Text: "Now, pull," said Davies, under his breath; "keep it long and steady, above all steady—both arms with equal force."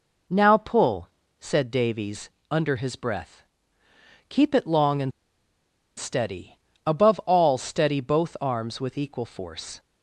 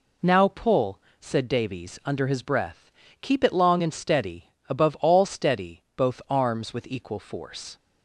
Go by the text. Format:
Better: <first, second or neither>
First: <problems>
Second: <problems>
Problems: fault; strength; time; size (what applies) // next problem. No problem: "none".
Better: second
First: pauses between "and" and "steady"; noticeable; at 5.1 s; 0.88 s long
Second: none